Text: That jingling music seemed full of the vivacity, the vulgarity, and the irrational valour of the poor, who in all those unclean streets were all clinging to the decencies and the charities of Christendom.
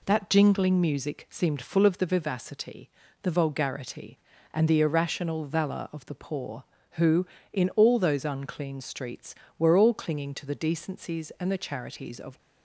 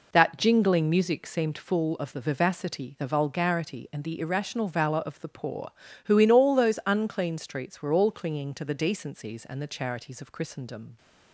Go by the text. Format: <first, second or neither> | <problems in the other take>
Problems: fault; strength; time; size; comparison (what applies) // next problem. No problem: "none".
second | stops before "Christendom"; at 12.3 s